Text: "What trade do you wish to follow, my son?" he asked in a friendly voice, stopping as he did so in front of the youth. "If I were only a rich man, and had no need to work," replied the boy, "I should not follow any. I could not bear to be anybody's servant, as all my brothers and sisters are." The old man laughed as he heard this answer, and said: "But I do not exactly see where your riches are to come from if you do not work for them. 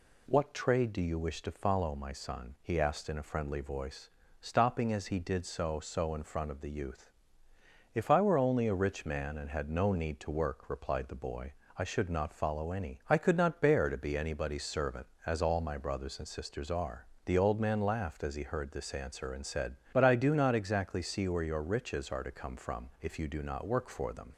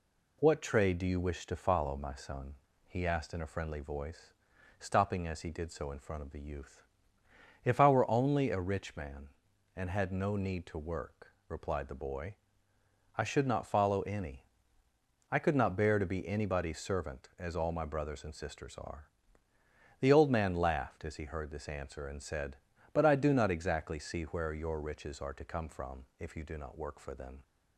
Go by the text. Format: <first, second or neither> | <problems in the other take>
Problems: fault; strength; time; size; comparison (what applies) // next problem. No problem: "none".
second | says "so" twice; at 5.7 s